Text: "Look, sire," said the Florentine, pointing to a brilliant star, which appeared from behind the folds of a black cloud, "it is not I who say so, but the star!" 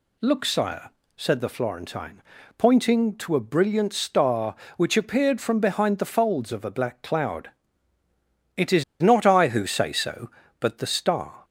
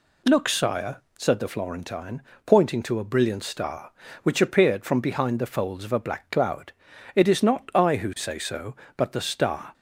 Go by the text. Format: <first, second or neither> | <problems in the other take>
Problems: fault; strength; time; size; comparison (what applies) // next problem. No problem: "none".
second | pauses between "is" and "not"; slight; at 8.8 s; 0.16 s long